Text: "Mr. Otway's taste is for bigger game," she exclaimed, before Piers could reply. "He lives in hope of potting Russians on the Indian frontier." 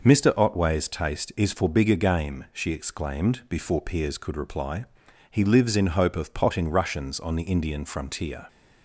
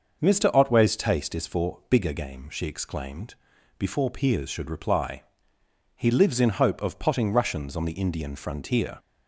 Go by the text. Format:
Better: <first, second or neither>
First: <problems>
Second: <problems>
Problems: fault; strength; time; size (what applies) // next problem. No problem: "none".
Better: first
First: none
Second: starts louder than the rest; noticeable; until 1.2 s; 6 dB // says "should" for "could"; at 4.4 s